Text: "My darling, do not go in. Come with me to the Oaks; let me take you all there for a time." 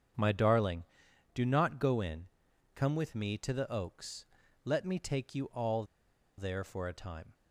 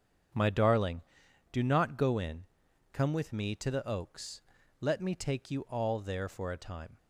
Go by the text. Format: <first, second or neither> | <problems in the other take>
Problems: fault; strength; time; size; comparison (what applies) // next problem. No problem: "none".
second | starts louder than the rest; strong; until 1.6 s; 8 dB; strong in the second // pauses between "all" and "there"; noticeable; at 5.8 s; 0.54 s long